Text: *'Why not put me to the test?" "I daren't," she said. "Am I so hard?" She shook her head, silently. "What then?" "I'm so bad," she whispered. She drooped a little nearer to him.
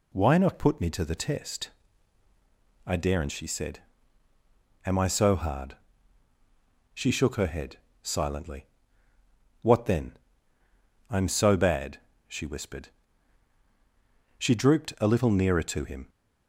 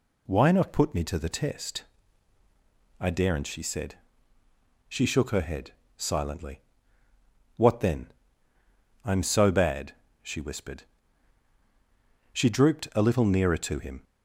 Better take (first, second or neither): first